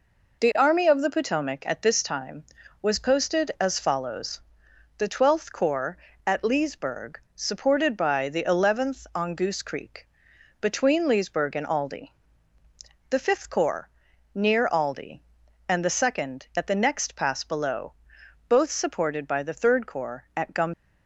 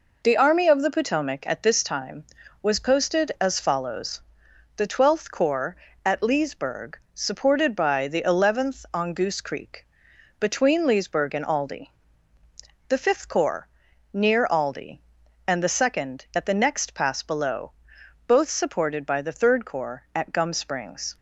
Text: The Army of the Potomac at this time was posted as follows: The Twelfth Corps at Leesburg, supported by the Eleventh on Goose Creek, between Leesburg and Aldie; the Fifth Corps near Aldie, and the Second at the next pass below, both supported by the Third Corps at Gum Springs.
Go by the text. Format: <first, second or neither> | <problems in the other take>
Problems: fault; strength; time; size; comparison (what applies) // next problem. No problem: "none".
second | pauses between "Corps" and "near"; at 13.8 s; 0.42 s long; also in the second // stops before "Springs"; at 20.7 s